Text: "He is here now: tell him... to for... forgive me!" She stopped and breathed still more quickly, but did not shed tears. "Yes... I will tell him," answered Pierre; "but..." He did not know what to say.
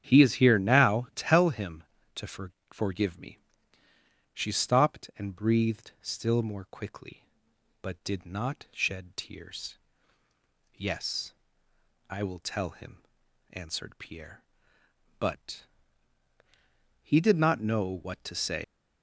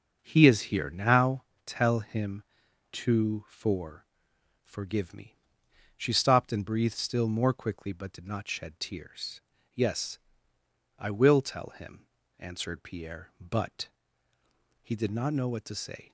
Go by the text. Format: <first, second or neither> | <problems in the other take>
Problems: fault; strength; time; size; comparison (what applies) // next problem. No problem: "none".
second | starts louder than the rest; strong; until 1.0 s; 9.5 dB; also in the second // pauses between "know" and "what"; slight; at 17.8 s; 0.16 s long // leaves "say" unfinished; at 18.6 s; 105 ms